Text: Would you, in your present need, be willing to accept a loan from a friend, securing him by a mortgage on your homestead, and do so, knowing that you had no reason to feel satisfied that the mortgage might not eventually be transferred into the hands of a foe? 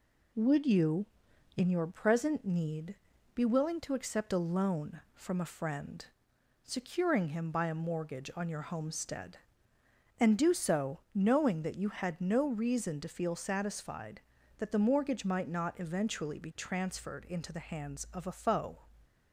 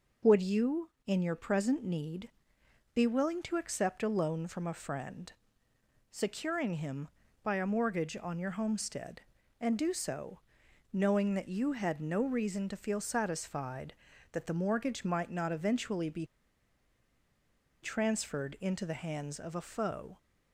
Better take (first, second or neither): first